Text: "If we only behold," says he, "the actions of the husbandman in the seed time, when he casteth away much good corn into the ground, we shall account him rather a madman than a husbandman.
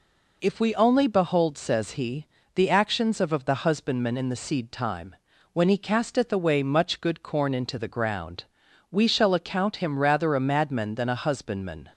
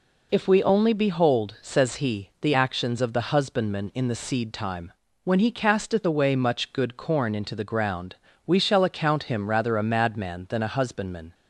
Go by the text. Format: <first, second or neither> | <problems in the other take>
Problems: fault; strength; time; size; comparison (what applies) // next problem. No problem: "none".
second | says "of" twice; at 3.3 s